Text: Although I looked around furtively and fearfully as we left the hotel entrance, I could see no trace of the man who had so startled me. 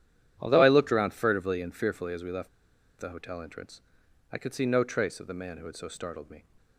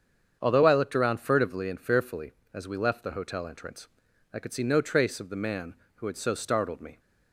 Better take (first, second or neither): second